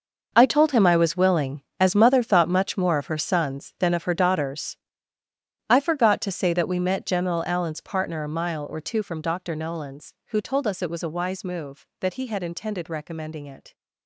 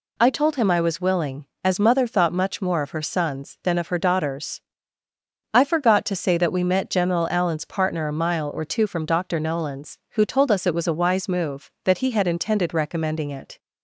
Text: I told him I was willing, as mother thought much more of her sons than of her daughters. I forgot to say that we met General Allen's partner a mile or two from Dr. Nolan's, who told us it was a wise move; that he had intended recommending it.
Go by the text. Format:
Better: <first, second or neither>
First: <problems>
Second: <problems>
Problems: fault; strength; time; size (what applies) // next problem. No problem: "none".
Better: second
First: gets quieter; strong; throughout; 13.5 dB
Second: none